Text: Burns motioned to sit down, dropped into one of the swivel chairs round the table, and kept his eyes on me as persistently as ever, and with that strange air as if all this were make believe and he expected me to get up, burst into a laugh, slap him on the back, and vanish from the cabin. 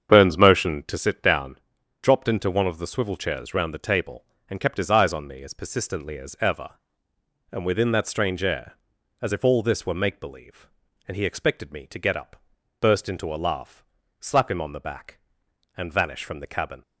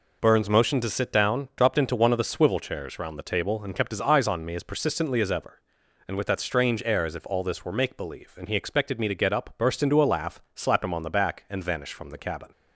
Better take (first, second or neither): second